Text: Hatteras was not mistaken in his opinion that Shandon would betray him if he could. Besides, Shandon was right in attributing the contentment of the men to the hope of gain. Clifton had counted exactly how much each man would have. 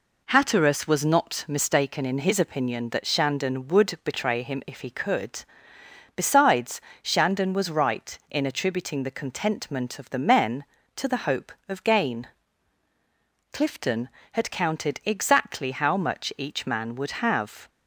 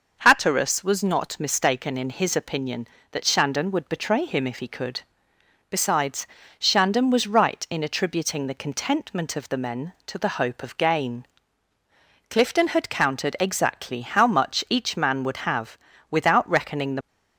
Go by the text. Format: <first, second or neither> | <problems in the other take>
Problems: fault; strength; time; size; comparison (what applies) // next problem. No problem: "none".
first | goes on to say "Without reckoning the"; noticeable; from 16.0 s on; 0.98 s long